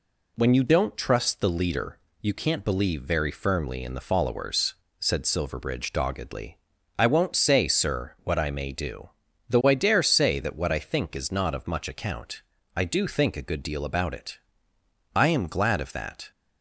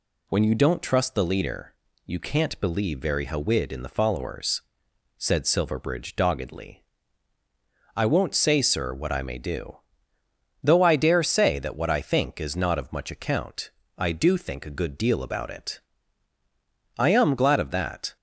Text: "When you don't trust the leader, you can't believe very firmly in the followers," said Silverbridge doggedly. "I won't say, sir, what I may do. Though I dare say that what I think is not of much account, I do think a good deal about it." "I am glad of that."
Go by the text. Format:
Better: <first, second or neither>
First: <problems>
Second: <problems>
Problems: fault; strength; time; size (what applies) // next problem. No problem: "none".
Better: first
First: none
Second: says "hawid" for "firmly"; at 3.2 s